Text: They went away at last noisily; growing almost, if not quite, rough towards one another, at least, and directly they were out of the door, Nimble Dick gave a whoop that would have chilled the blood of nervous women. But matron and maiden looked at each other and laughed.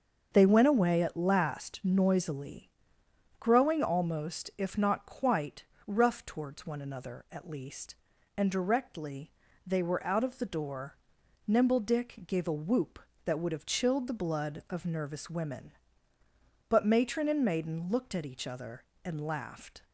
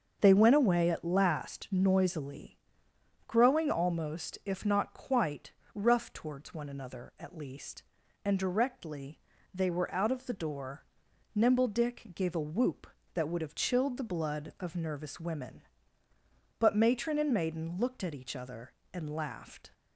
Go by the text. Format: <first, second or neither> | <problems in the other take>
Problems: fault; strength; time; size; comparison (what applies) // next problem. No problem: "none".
neither | starts louder than the rest; the same in both // pauses between "directly" and "they"; slight; the same in both